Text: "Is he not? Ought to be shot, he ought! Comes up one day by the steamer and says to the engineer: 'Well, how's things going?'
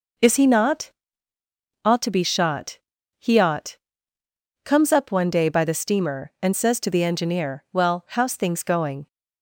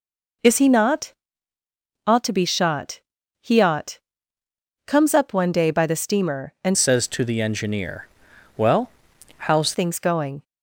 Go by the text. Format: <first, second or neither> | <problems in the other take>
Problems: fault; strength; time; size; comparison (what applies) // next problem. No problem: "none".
first | changes voice from "says" to "how's"; from 6.7 to 9.7 s; 3.0 s long